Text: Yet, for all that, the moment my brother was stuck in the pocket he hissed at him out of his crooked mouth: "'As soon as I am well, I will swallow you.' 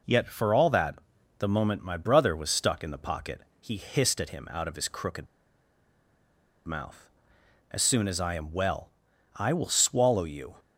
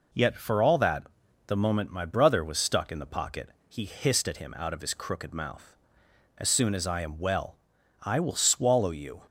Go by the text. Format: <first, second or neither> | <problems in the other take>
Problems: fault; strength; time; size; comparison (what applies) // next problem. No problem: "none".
second | pauses between "pocket" and "he"; slight; at 3.4 s; 0.18 s long; slight in the second // pauses between "crooked" and "mouth"; strong; at 5.2 s; 1.4 s long